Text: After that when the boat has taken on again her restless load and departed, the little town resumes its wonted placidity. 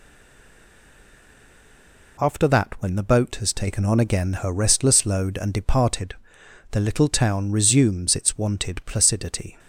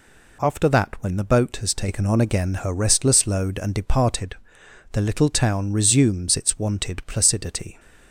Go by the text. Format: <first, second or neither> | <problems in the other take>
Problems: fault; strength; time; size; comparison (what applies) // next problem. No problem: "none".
second | stays silent before the first word; until 2.1 s; 2.1 s long